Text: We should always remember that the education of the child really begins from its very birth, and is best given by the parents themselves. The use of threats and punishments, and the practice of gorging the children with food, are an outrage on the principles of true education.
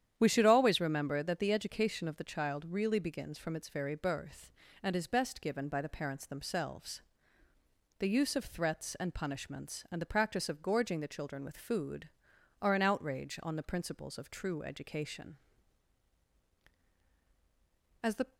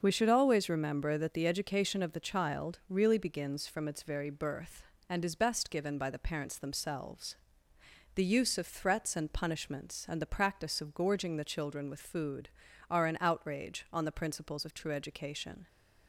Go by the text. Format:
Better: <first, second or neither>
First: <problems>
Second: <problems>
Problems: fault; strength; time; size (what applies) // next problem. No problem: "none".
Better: second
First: starts louder than the rest; strong; until 1.2 s; 10 dB // goes on to say "As the"; slight; from 18.0 s on; 0.34 s long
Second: starts louder than the rest; until 1.0 s; 6.5 dB